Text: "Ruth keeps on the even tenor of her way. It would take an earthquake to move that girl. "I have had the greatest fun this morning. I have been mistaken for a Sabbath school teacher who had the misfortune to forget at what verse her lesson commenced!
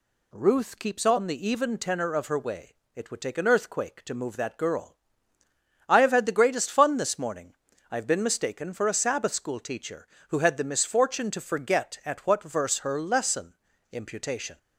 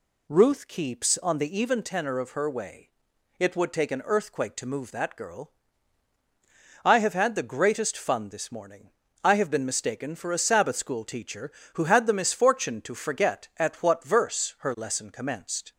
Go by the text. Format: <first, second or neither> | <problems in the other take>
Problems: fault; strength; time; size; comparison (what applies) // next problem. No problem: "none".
second | says "imputation" for "commenced"; at 13.8 s